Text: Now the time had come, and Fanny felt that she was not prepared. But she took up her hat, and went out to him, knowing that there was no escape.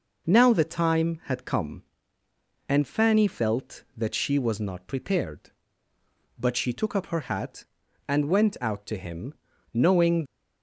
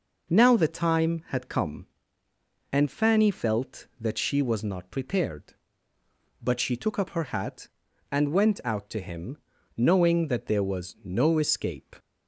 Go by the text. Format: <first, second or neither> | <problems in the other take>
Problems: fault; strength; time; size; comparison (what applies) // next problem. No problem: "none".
second | stops before "that there was no escape"; at 10.2 s